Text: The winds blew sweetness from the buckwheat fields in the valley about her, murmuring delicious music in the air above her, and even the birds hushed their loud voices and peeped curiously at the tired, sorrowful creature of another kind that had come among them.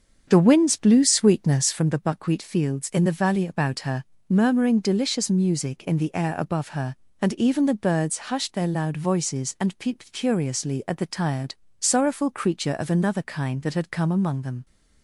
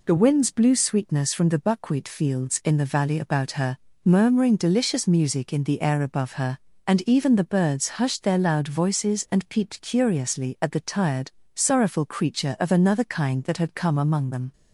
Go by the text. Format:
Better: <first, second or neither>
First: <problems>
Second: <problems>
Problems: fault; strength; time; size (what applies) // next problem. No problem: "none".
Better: second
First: starts louder than the rest; strong; until 1.9 s; 7 dB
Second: none